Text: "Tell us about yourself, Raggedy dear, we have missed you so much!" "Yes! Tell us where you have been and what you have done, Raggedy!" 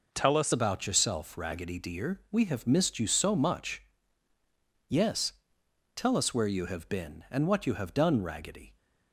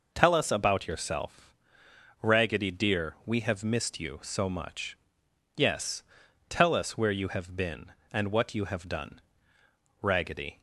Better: second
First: changes voice at "about"; from 0.5 s on; 8.2 s long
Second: none

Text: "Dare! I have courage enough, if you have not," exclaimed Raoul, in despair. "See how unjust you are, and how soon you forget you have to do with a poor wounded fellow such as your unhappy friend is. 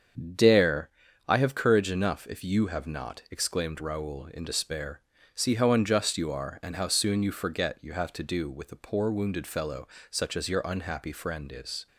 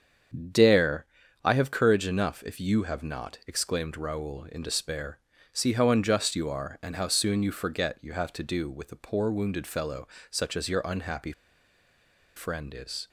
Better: first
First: starts louder than the rest; strong; until 1.7 s; 8 dB // pauses between "fellow" and "such"; slight; at 9.8 s; 0.22 s long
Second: starts louder than the rest; strong; until 1.9 s; 8 dB // pauses between "fellow" and "such"; slight; at 10.0 s; 0.22 s long // pauses between "unhappy" and "friend"; at 11.3 s; 1.0 s long

